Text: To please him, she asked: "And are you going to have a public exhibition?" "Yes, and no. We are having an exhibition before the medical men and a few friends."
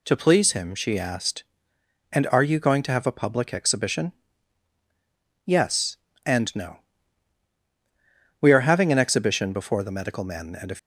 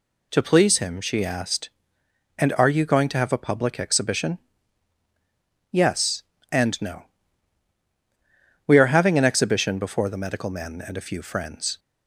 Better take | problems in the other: second | stops before "few friends"; at 10.7 s

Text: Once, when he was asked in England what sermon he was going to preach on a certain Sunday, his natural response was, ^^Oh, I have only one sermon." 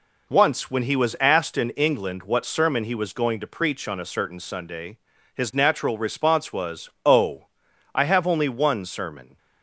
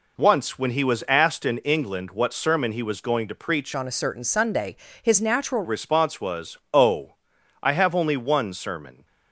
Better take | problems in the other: first | changes voice from "on" to "natural"; from 3.7 to 5.6 s; 1.9 s long

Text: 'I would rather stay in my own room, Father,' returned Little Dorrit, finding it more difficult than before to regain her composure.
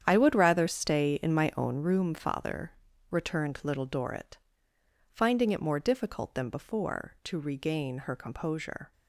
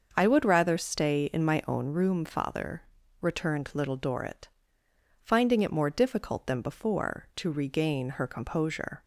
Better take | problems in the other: second | gets quieter; strong; throughout; 13 dB // starts louder than the rest; strong; until 1.0 s; 9 dB; also in the second

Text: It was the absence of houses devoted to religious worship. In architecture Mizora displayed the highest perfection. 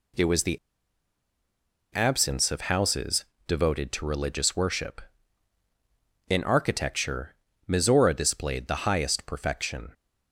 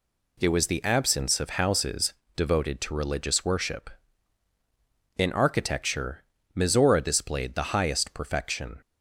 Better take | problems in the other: second | pauses between "the" and "absence"; strong; at 0.5 s; 1.3 s long // pauses between "houses" and "devoted"; slight; at 3.2 s; 0.22 s long; slight in the second // pauses between "architecture" and "Mizora"; slight; at 7.3 s; 0.32 s long; slight in the second

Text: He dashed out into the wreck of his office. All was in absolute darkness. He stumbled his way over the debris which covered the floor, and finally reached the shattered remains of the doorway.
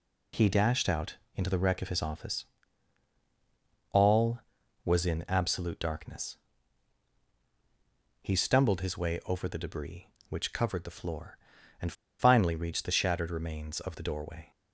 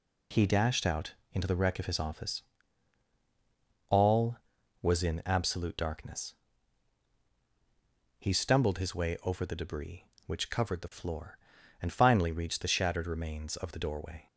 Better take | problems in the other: second | pauses between "out" and "into"; slight; at 1.1 s; 0.22 s long; slight in the second // pauses between "and" and "finally"; slight; at 11.9 s; 0.27 s long

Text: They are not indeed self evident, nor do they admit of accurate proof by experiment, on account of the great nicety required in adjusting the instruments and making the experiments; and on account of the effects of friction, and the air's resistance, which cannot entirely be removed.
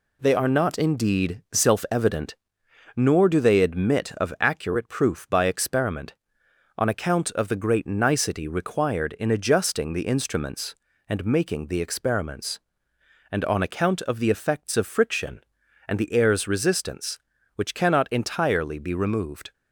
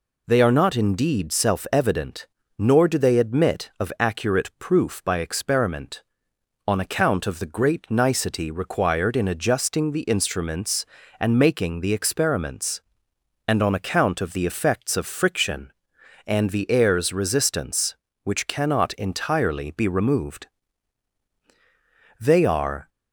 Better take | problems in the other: first | goes on to say "They are"; noticeable; from 22.1 s on; 0.70 s long

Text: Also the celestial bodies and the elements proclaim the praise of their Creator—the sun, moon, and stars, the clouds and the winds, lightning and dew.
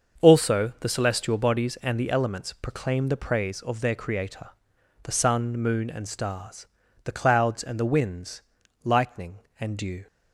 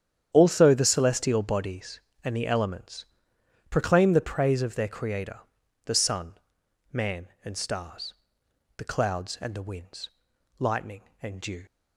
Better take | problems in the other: first | starts louder than the rest; strong; until 1.3 s; 9 dB; also in the first // pauses between "elements" and "proclaim"; noticeable; at 3.0 s; 0.66 s long // says "man" for "moon"; at 6.9 s

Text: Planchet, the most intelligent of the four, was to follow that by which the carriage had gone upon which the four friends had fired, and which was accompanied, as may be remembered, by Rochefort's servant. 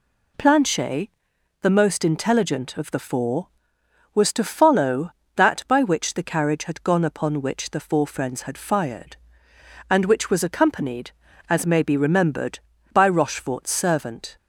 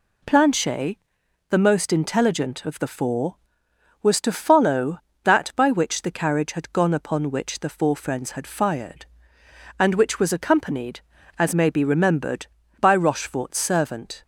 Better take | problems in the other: neither | none

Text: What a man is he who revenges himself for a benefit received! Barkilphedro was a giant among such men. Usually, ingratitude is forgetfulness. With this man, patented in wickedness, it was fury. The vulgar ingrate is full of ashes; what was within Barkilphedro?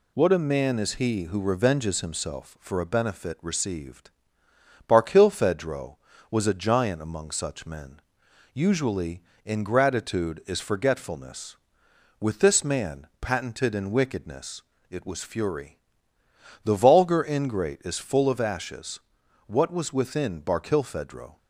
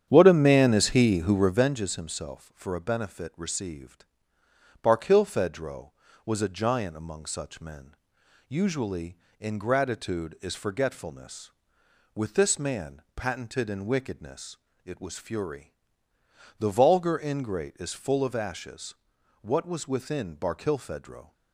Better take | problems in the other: first | starts louder than the rest; strong; until 1.7 s; 9 dB

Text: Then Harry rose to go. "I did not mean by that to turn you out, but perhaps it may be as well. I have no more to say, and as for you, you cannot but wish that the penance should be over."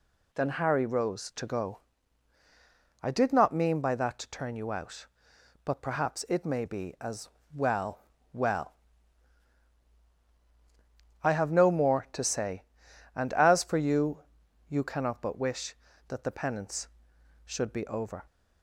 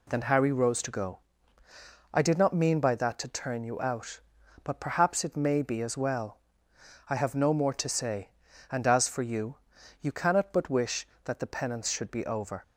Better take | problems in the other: second | pauses between "as" and "well"; slight; at 7.2 s; 0.26 s long // says "well" twice; at 8.3 s

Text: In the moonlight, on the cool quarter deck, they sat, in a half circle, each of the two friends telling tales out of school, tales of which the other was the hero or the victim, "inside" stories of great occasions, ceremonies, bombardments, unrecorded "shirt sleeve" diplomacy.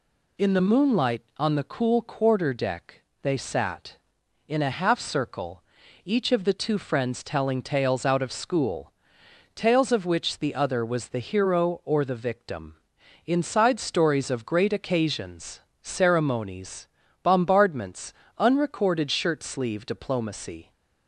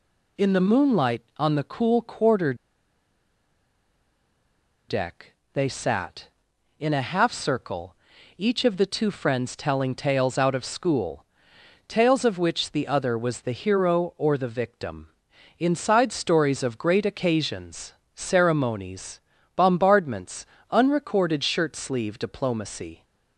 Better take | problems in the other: first | pauses between "quarter" and "deck"; strong; at 2.5 s; 2.3 s long

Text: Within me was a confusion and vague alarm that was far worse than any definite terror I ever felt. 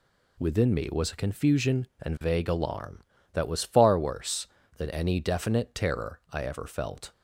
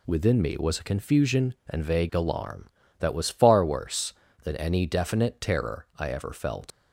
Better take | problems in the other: first | leaves "felt" unfinished; at 6.7 s; 80 ms

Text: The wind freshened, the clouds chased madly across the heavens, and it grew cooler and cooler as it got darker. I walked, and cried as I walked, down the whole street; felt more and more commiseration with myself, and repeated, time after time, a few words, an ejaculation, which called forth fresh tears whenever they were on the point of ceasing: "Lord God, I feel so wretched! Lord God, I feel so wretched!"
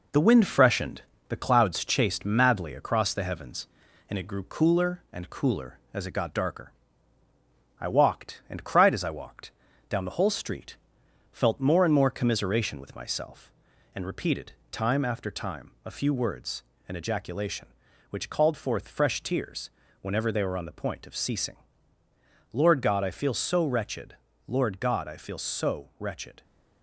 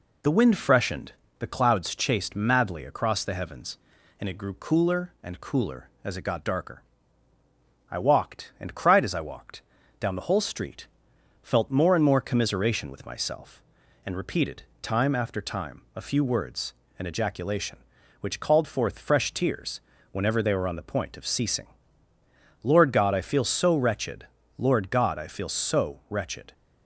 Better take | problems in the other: second | gets quieter; throughout; 3.5 dB // pauses between "tears" and "whenever"; slight; at 19.7 s; 0.30 s long; slight in the second

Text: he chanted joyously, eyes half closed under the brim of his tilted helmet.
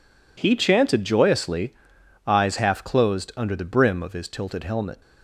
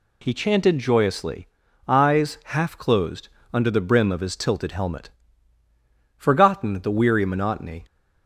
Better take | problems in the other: first | pauses between "closed" and "under"; slight; at 3.2 s; 0.26 s long // goes on to say "Forgotten the weary monotony"; from 6.1 s on; 1.6 s long

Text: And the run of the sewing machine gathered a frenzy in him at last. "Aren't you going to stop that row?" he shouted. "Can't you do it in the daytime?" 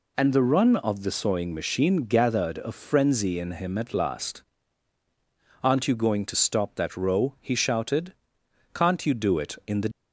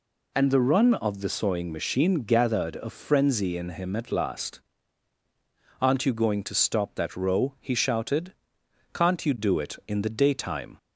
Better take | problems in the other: second | stops before "daytime"; at 9.9 s

